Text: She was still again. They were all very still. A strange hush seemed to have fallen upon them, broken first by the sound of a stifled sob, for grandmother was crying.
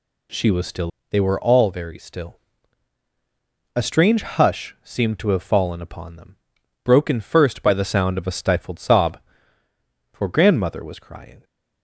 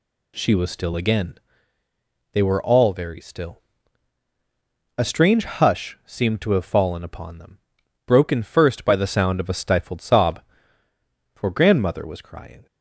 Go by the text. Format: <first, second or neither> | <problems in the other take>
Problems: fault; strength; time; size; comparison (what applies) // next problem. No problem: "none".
second | skips "again"; at 0.9 s